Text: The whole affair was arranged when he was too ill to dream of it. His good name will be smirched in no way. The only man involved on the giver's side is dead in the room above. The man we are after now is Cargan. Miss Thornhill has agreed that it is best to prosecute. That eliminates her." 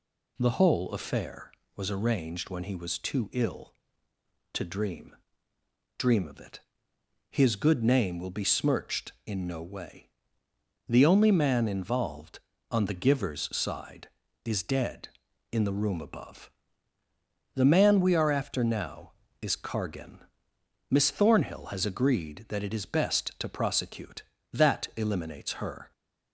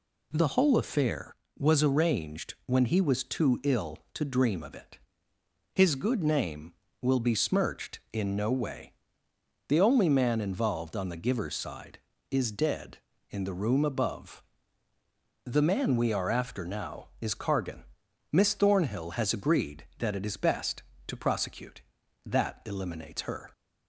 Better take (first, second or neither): second